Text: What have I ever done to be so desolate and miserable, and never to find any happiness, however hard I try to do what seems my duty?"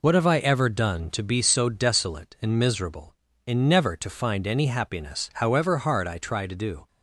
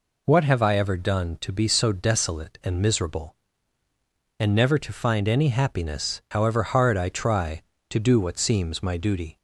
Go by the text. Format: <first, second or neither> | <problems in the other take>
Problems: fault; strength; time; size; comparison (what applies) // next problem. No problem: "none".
second | stops before "what seems my duty"; at 6.8 s